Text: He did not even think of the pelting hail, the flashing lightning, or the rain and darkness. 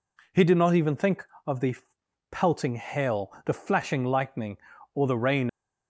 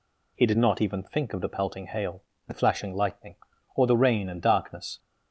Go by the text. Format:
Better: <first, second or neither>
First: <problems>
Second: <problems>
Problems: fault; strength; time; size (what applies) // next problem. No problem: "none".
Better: second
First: pauses between "the" and "pelting"; noticeable; at 1.7 s; 0.58 s long // stops before "and darkness"; at 5.4 s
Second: none